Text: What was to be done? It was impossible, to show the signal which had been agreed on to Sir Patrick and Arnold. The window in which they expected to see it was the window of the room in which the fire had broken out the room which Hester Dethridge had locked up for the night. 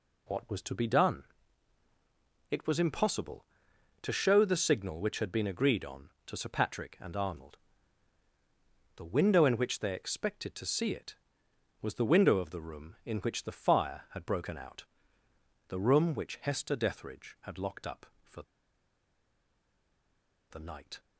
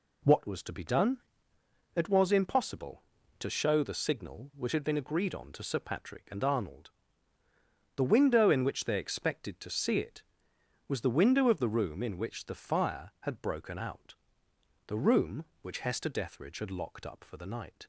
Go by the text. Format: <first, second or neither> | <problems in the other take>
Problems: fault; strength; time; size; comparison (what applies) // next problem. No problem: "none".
second | pauses between "out" and "the"; noticeable; at 14.8 s; 0.86 s long; noticeable in the second // pauses between "for" and "the"; strong; at 18.4 s; 2.0 s long